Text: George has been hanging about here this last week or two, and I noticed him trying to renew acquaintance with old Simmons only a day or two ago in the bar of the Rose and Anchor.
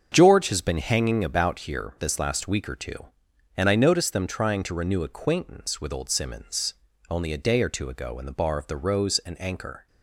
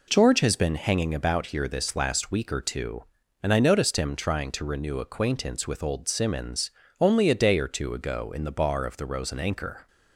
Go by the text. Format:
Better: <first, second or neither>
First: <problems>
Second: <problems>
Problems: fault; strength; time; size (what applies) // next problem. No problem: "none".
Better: second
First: starts louder than the rest; until 1.1 s; 7 dB // says "them" for "him"; at 4.1 s // pauses between "Simmons" and "only"; slight; at 6.7 s; 0.34 s long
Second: pauses between "Simmons" and "only"; slight; at 6.7 s; 0.28 s long